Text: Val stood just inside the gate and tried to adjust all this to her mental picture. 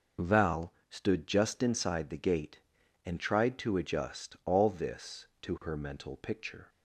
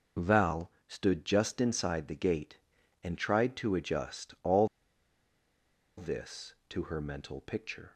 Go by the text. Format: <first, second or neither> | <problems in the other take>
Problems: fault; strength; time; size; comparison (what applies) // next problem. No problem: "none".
first | pauses between "Val" and "stood"; slight; at 0.7 s; 0.16 s long; slight in the first // pauses between "all" and "this"; strong; at 4.6 s; 1.3 s long